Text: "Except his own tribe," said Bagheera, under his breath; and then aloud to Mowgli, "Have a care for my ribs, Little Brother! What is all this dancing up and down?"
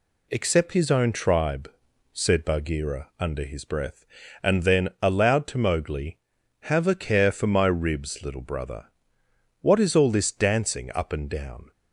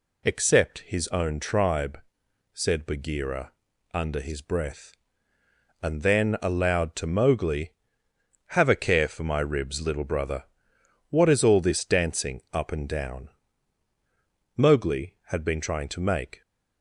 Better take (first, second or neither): first